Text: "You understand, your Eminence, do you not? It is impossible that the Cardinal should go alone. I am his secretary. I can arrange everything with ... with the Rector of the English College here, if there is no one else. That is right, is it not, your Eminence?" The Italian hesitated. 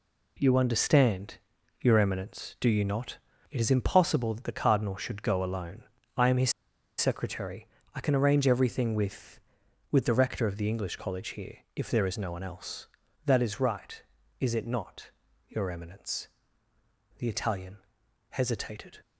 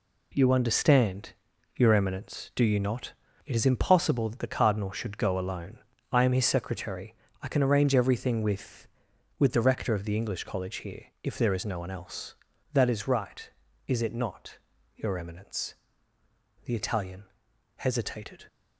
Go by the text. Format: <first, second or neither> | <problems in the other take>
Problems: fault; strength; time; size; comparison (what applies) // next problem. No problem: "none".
second | pauses between "his" and "secretary"; noticeable; at 6.5 s; 0.46 s long // pauses between "Italian" and "hesitated"; noticeable; at 17.7 s; 0.54 s long; noticeable in the second